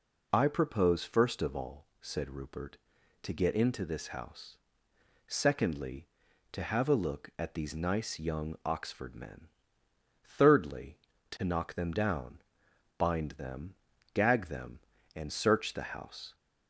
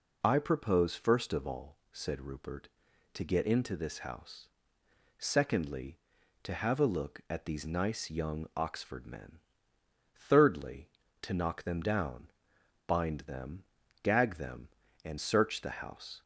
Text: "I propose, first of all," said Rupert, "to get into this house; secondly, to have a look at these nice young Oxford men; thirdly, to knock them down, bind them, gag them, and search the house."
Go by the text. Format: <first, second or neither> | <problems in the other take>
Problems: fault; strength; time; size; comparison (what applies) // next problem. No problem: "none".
neither | none